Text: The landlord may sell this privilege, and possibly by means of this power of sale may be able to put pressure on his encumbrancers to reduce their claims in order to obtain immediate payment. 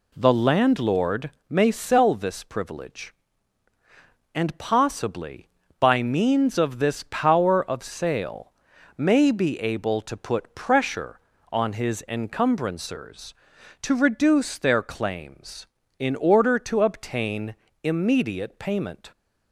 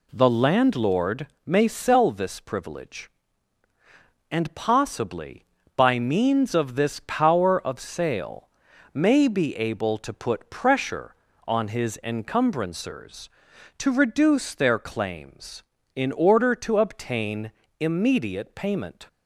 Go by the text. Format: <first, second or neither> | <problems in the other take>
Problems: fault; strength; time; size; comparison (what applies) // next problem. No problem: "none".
neither | pauses between "landlord" and "may"; slight; the same in both // pauses between "sale" and "may"; noticeable; the same in both // pauses between "obtain" and "immediate"; slight; the same in both